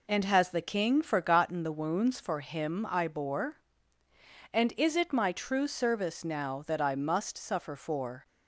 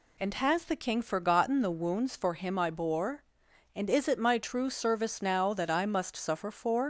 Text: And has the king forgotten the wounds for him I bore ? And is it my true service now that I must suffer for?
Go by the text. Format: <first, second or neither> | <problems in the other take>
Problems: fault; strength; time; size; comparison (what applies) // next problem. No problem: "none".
first | leaves "for" unfinished; at 6.8 s; 115 ms